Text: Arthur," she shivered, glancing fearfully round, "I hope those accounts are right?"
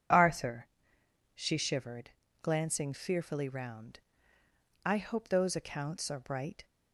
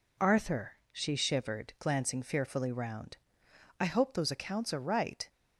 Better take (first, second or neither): second